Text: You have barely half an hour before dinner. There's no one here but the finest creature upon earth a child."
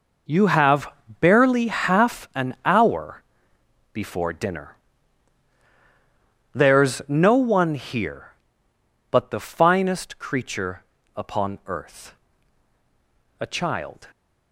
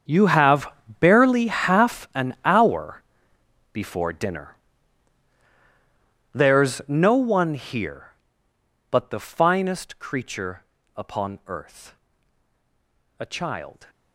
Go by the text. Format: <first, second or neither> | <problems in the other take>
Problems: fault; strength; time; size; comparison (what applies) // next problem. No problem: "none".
first | gets quieter; strong; throughout; 18.5 dB // pauses between "have" and "barely"; slight; at 0.7 s; 0.30 s long; slight in the first // pauses between "hour" and "before"; noticeable; at 3.0 s; 0.70 s long; noticeable in the first // pauses between "creature" and "upon"; slight; at 10.6 s; 0.32 s long; slight in the first // pauses between "earth" and "a"; at 11.9 s; 1.2 s long; also in the first